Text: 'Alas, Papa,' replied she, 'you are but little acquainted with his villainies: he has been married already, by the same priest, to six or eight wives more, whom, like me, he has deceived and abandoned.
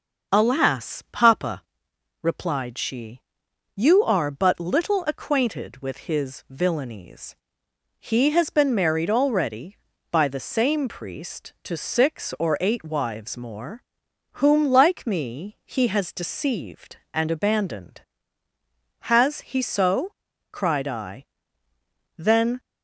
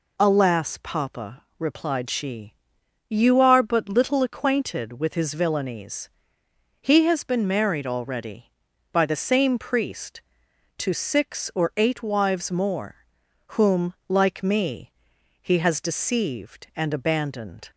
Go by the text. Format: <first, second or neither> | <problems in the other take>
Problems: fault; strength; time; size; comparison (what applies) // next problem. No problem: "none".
second | starts louder than the rest; noticeable; until 1.4 s; 6 dB // goes on to say "Has he so cried I then"; strong; from 18.9 s on; 3.6 s long